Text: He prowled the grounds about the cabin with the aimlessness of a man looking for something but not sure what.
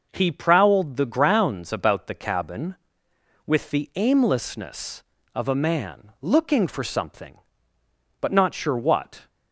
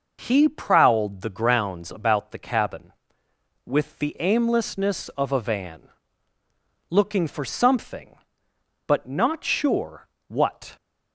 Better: first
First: none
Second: says "van" for "man"; at 5.3 s // pauses between "sure" and "what"; slight; at 10.0 s; 0.20 s long

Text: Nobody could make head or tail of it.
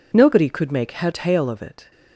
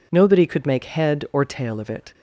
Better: second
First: skips "or"; at 1.1 s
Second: none

